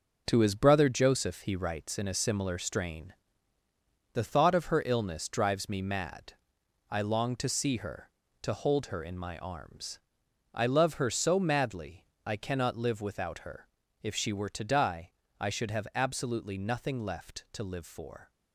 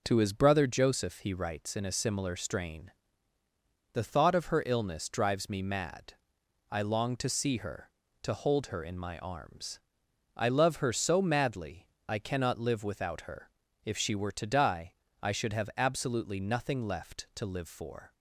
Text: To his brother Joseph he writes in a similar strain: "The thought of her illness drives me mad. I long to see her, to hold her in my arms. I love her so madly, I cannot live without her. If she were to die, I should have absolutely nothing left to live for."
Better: second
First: gets quieter; strong; throughout; 7.5 dB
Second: none

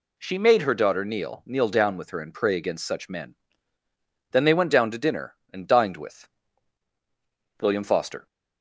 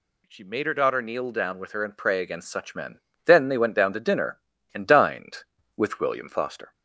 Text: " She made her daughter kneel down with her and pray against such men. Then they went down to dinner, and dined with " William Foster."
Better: second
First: says "kneel" twice; at 1.4 s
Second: none

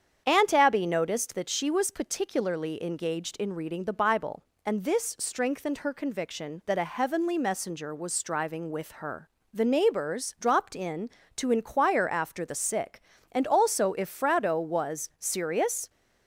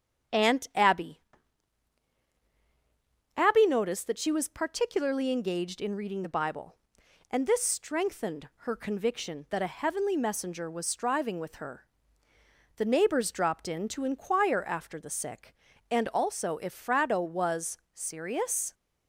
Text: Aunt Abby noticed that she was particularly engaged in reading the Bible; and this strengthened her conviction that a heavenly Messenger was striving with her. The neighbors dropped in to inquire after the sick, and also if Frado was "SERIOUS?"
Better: first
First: starts louder than the rest; strong; until 1.2 s; 8 dB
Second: starts louder than the rest; strong; until 3.5 s; 8.5 dB // says "Abby" twice; at 3.3 s // pauses between "was" and "SERIOUS"; slight; at 17.7 s; 0.16 s long

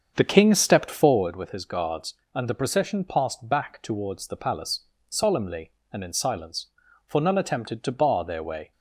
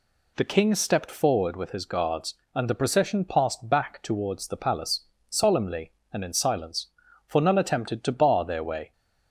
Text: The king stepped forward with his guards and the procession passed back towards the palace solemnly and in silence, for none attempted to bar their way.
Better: second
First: starts louder than the rest; strong; until 1.3 s; 7 dB // pauses between "palace" and "solemnly"; slight; at 4.8 s; 0.26 s long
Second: pauses between "palace" and "solemnly"; slight; at 5.0 s; 0.26 s long

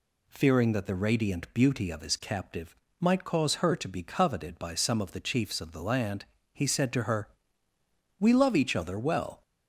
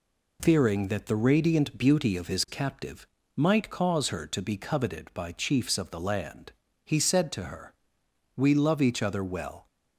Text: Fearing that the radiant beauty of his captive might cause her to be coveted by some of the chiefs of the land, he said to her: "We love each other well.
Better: first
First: pauses between "captive" and "might"; slight; at 2.7 s; 0.24 s long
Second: pauses between "captive" and "might"; slight; at 3.0 s; 0.28 s long // skips "some of the"; at 5.3 s

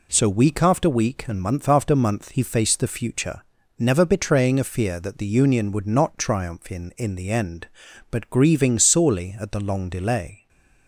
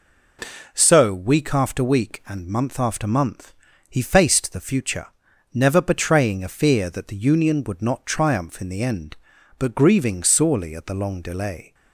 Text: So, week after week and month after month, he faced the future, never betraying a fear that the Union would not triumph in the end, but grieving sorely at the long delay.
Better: second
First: says "in" twice; at 6.9 s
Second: none

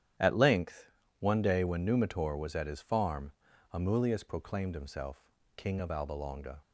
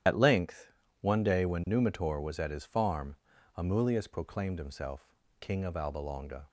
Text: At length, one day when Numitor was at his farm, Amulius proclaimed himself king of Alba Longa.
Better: first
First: starts louder than the rest; strong; until 1.4 s; 10 dB // pauses between "himself" and "king"; slight; at 5.3 s; 0.26 s long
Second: loses the start of "At"; at 0.0 s; 55 ms // starts louder than the rest; strong; until 1.3 s; 10.5 dB // pauses between "himself" and "king"; slight; at 5.1 s; 0.26 s long

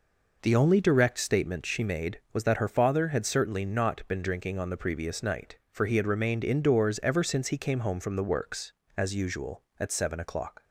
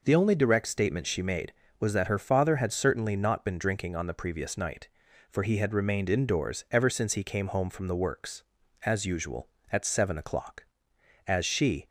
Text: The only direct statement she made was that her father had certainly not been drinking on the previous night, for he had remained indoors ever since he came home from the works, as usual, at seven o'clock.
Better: first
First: none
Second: goes on to say "As she"; from 11.2 s on; 0.60 s long

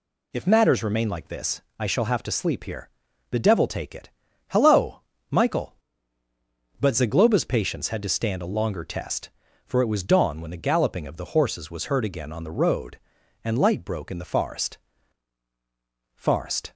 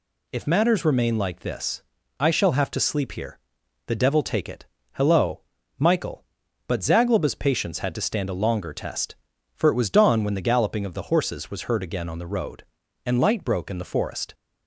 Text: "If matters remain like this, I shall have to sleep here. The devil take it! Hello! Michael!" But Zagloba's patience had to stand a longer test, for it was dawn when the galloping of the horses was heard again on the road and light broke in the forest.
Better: second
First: says "forest" twice; at 16.1 s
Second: none

